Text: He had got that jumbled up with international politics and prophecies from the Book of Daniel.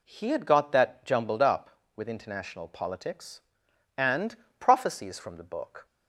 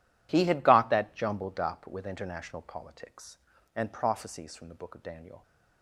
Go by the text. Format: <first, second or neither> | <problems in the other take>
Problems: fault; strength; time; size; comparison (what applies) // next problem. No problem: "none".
second | pauses between "and" and "prophecies"; slight; at 4.3 s; 0.22 s long // stops before "of Daniel"; at 5.8 s